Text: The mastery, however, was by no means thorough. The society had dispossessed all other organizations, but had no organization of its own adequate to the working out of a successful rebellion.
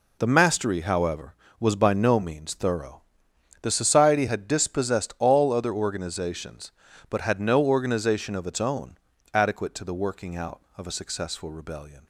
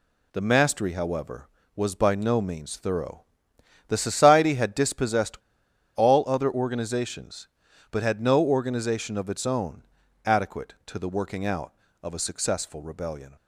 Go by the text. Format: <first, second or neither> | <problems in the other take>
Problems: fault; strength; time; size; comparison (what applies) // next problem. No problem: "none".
first | pauses between "dispossessed" and "all"; noticeable; at 5.3 s; 0.59 s long // pauses between "own" and "adequate"; at 9.8 s; 0.42 s long; also in the first